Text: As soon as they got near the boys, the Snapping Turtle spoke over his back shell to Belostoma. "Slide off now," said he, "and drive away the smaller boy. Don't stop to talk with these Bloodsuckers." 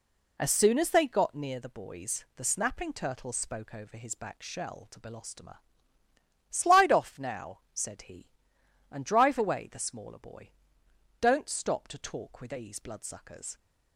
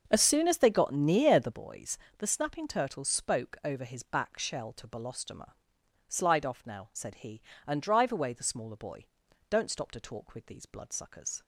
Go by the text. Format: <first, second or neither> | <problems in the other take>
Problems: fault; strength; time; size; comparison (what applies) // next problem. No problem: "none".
first | starts louder than the rest; noticeable; until 1.6 s; 6 dB